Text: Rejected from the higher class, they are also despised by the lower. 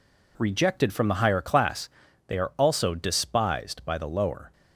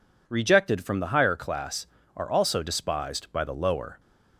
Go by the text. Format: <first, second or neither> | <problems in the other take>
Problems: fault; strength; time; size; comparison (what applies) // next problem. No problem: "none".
first | skips "they"; at 2.0 s